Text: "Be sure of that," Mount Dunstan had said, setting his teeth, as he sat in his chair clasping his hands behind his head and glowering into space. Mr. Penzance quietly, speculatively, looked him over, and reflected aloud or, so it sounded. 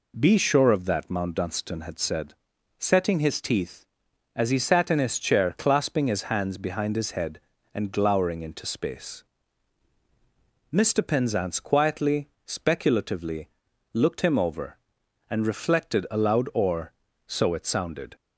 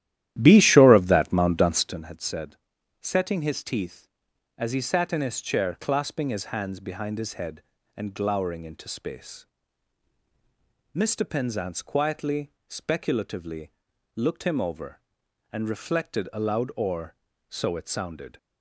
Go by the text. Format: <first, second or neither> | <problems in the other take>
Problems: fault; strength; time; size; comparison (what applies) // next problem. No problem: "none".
first | starts louder than the rest; strong; until 2.0 s; 13 dB